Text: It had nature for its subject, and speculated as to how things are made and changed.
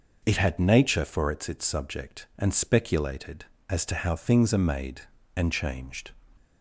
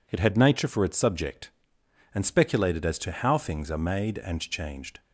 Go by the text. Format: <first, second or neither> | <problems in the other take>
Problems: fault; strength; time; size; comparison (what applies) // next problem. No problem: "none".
second | says "its" twice; at 1.4 s